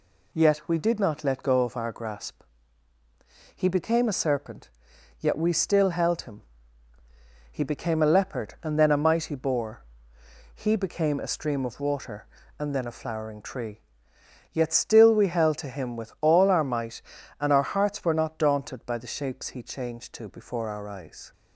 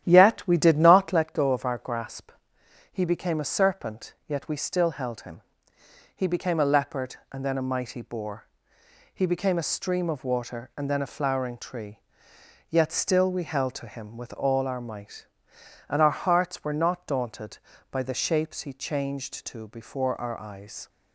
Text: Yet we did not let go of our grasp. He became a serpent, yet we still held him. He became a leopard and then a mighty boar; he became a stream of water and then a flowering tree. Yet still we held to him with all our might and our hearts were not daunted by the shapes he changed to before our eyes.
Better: first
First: none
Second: starts louder than the rest; strong; until 1.2 s; 11 dB

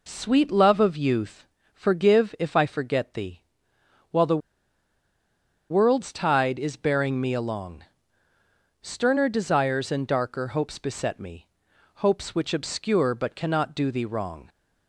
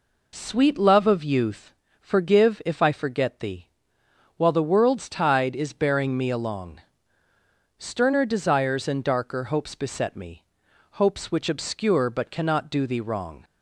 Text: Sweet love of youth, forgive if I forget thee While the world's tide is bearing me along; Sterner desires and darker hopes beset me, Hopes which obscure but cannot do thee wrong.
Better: second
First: pauses between "thee" and "While"; noticeable; at 3.4 s; 0.68 s long // pauses between "the" and "world's"; strong; at 4.4 s; 1.3 s long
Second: pauses between "thee" and "While"; noticeable; at 3.6 s; 0.68 s long

